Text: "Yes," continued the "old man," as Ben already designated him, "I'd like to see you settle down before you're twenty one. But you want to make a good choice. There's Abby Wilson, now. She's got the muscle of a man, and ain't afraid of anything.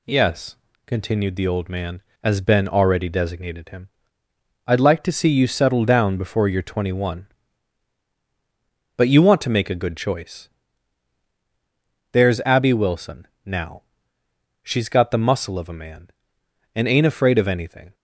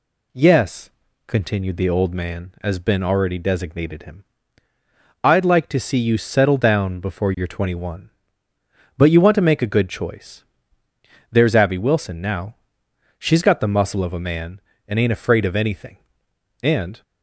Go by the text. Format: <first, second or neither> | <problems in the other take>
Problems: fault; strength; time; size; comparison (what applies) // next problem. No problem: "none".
first | goes on to say "And"; slight; from 16.6 s on; 0.40 s long